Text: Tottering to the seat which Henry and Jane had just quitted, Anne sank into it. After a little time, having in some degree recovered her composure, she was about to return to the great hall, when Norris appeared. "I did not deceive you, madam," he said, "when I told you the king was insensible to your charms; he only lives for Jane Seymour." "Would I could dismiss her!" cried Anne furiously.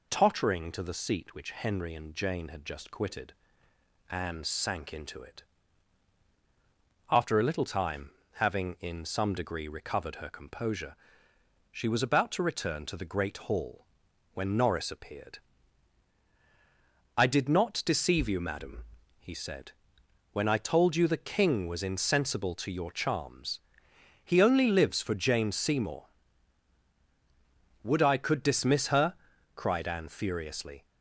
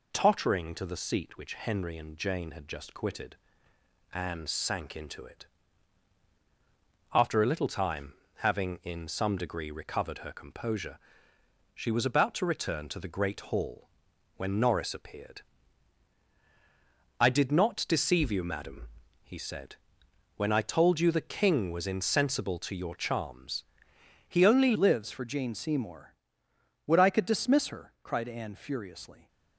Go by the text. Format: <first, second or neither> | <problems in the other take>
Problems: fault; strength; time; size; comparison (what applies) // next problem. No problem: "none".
first | changes voice at "lives"; from 24.7 s on; 4.5 s long